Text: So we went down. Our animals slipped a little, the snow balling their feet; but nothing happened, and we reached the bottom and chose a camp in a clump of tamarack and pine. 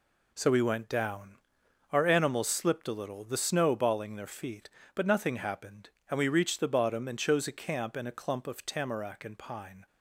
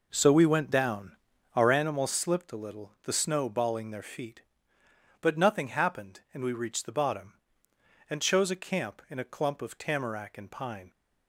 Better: first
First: none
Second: starts louder than the rest; noticeable; until 2.0 s; 5 dB

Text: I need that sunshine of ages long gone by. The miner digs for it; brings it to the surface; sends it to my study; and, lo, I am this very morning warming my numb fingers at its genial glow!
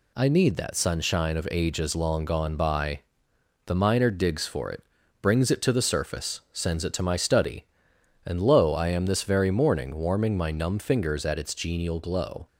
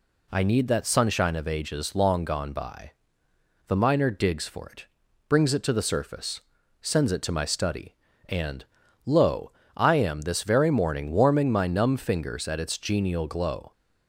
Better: neither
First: none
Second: none

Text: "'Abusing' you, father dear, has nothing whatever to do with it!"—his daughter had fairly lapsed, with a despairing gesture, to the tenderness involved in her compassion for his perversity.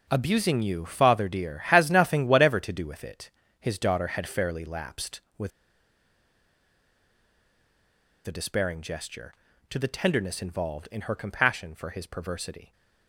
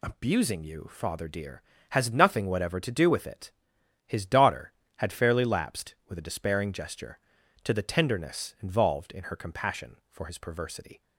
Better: second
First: pauses between "with" and "a"; strong; at 5.5 s; 2.7 s long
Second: none

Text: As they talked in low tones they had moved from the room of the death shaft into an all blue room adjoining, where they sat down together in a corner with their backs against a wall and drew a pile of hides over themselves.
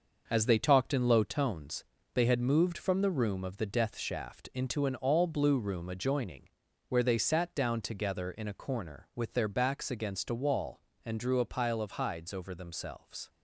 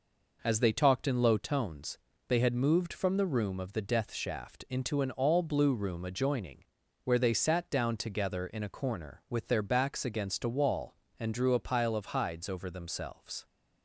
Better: second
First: gets quieter; throughout; 6 dB // pauses between "tones" and "they"; slight; at 1.8 s; 0.30 s long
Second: pauses between "tones" and "they"; slight; at 1.9 s; 0.30 s long

